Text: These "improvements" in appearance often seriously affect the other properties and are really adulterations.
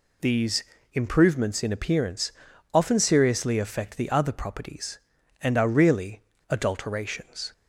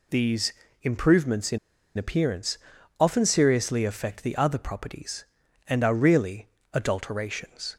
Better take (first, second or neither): first